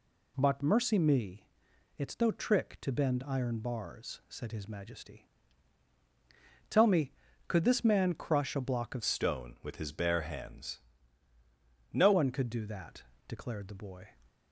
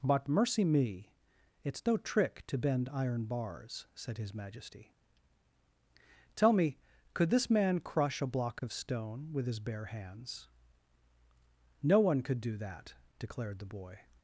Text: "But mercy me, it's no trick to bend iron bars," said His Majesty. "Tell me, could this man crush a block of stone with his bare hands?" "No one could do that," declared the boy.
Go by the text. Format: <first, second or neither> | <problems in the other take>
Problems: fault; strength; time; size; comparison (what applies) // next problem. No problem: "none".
second | changes voice from "stone" to "No"; from 9.0 to 12.1 s; 3.1 s long